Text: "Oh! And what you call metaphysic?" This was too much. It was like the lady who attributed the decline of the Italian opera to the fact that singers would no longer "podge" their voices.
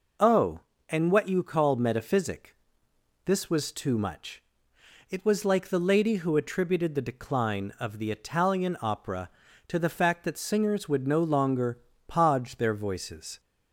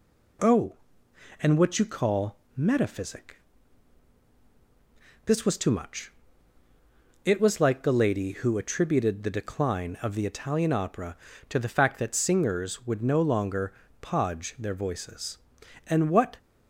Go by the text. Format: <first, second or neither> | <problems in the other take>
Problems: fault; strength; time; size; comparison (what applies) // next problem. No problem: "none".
first | pauses between "call" and "metaphysic"; slight; at 2.3 s; 0.18 s long // pauses between "longer" and "podge"; slight; at 13.7 s; 0.26 s long; slight in the first // goes on to say "And what"; from 15.8 s on; 0.52 s long